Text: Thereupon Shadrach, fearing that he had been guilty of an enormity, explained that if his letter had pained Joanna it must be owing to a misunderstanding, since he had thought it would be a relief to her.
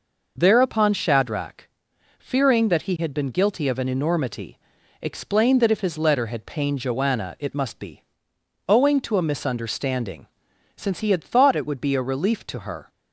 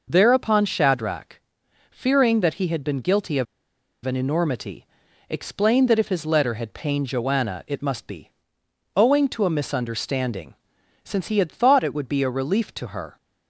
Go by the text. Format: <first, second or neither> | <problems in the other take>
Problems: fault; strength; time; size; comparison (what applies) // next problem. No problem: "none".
first | pauses between "of" and "an"; noticeable; at 3.4 s; 0.58 s long // pauses between "be" and "owing"; noticeable; at 8.3 s; 0.66 s long; noticeable in the first